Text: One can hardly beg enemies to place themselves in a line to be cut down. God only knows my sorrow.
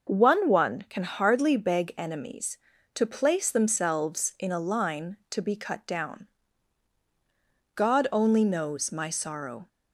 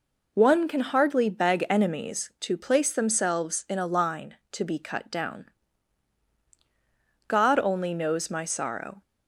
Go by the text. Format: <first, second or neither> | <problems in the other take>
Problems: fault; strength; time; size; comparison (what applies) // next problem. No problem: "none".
second | says "One" twice; at 0.4 s